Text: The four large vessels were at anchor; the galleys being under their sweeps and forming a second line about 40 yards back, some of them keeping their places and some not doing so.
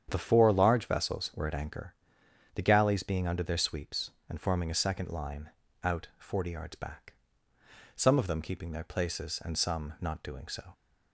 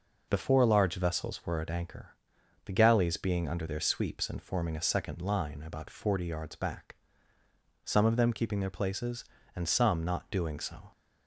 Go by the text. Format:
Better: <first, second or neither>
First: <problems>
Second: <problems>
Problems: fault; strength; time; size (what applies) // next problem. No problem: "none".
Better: second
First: starts louder than the rest; strong; until 1.1 s; 8.5 dB // says "out" for "about"; at 5.8 s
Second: none